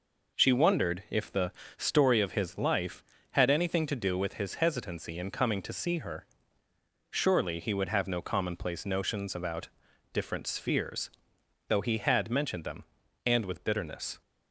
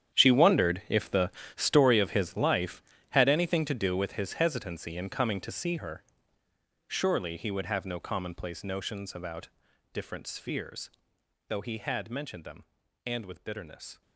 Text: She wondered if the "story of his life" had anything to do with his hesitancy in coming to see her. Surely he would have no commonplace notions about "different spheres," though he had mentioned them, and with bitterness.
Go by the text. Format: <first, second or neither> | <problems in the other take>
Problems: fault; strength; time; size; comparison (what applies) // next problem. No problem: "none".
first | gets quieter; strong; throughout; 16 dB // pauses between "the" and "story"; slight; at 1.3 s; 0.26 s long; slight in the first // pauses between "about" and "different"; noticeable; at 9.4 s; 0.46 s long; noticeable in the first